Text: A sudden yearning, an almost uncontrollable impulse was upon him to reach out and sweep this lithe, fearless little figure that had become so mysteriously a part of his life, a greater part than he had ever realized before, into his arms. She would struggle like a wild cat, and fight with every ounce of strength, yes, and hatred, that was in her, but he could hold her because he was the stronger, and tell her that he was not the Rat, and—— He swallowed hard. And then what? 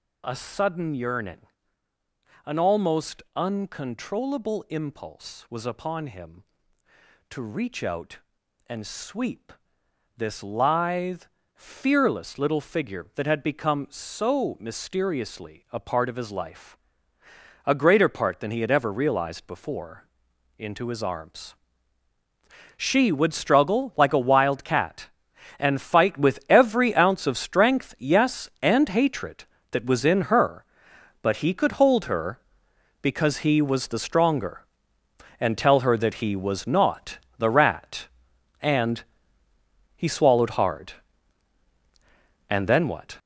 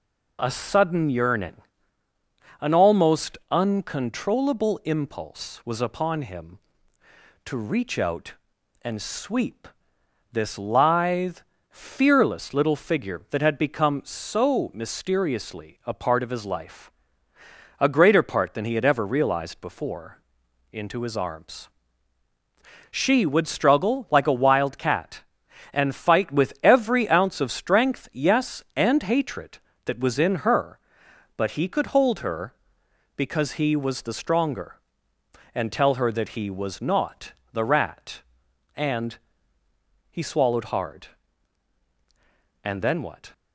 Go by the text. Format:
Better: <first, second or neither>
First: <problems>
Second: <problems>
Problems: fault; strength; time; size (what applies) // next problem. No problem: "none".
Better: second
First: gets louder; strong; throughout; 8.5 dB // pauses between "almost" and "uncontrollable"; slight; at 3.2 s; 0.16 s long // pauses between "sweep" and "this"; noticeable; at 9.5 s; 0.64 s long // pauses between "not" and "the"; slight; at 37.1 s; 0.20 s long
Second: pauses between "almost" and "uncontrollable"; slight; at 3.3 s; 0.16 s long // pauses between "sweep" and "this"; noticeable; at 9.6 s; 0.64 s long // pauses between "not" and "the"; slight; at 37.3 s; 0.20 s long